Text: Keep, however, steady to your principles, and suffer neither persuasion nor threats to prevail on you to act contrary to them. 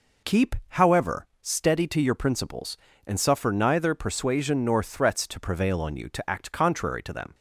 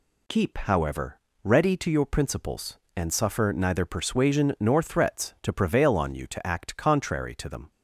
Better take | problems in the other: first | says "ready" for "steady"; at 1.4 s

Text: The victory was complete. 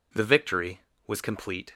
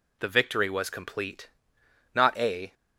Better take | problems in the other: first | goes on to say "Not a"; from 2.1 s on; 0.60 s long

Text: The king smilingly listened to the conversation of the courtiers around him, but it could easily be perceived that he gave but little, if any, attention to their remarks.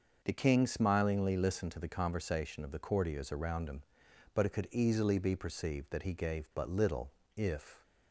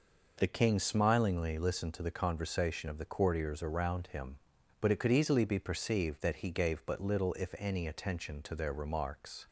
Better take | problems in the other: second | starts louder than the rest; until 1.2 s; 6 dB // stops before "any attention to their remarks"; at 7.8 s

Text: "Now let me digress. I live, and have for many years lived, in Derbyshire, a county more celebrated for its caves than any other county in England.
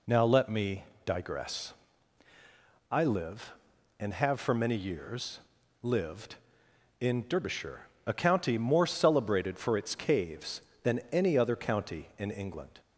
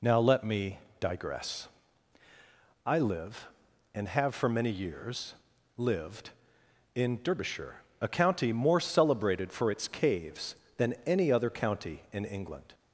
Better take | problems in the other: neither | pauses between "me" and "digress"; slight; the same in both // pauses between "years" and "lived"; the same in both

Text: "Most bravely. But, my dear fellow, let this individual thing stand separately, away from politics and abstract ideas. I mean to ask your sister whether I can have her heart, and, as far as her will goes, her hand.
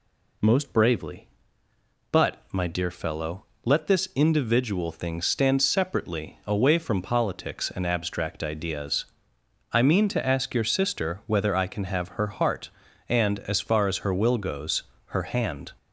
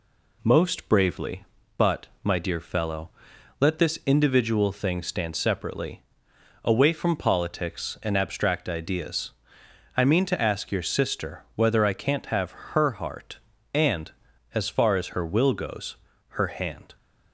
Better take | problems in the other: first | says "can't" for "can"; at 11.9 s

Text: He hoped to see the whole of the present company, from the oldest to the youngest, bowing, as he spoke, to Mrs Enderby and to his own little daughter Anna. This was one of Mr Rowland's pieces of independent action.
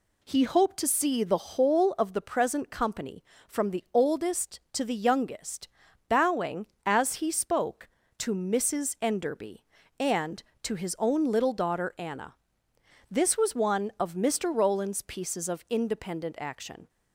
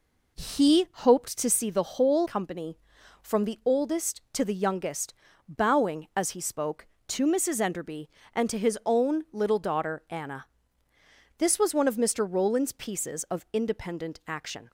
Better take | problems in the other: first | skips "of the present"; at 2.2 s

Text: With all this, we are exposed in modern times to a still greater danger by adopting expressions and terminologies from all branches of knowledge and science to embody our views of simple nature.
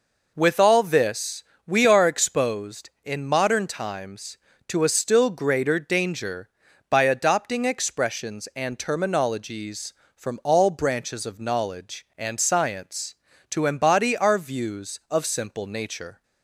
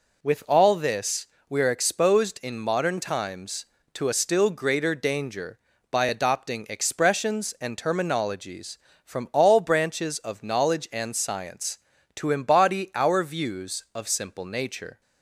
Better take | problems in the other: neither | none

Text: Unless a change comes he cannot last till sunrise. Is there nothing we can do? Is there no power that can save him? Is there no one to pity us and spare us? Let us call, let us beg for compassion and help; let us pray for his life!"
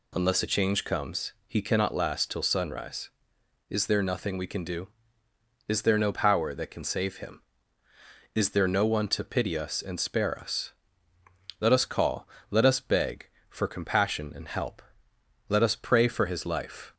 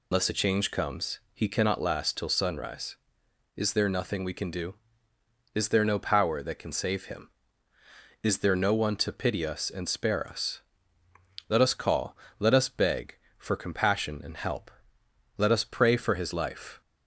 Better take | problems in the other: first | loses the start of "Unless"; at 0.1 s; 120 ms // pauses between "comes" and "he"; slight; at 1.1 s; 0.16 s long; slight in the first

